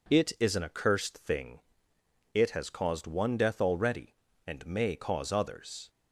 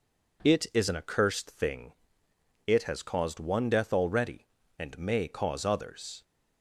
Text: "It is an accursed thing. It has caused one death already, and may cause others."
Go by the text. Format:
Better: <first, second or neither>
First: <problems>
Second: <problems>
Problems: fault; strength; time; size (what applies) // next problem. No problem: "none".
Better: neither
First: none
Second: none